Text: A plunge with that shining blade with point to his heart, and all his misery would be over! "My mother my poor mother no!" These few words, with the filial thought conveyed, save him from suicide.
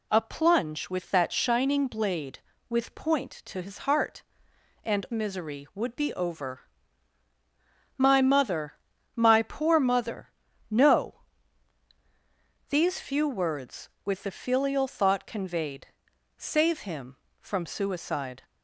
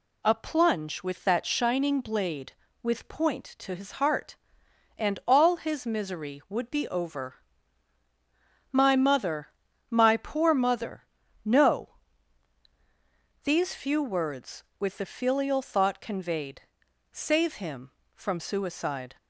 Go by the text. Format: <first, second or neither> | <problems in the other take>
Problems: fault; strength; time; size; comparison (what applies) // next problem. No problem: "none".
second | skips "all his"; at 5.0 s // pauses between "mother" and "my"; slight; at 8.7 s; 0.36 s long; slight in the second // pauses between "mother" and "no"; at 10.3 s; 0.40 s long; also in the second